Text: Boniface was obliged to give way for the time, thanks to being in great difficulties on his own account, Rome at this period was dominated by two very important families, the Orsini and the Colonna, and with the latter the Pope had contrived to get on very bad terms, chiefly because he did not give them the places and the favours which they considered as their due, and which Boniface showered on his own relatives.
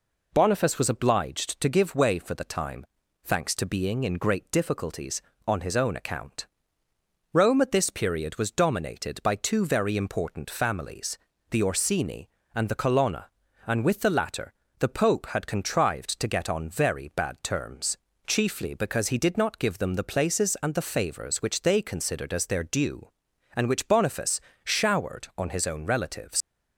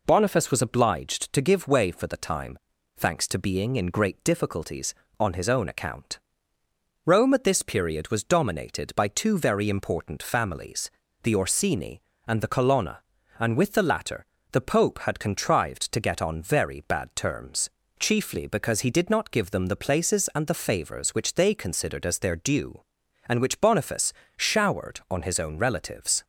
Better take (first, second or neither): second